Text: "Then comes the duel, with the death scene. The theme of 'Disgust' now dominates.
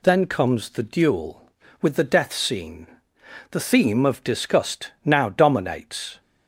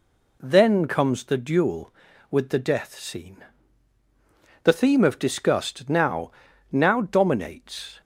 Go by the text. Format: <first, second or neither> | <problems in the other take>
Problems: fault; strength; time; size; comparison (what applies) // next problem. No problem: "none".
first | says "now" twice; at 6.7 s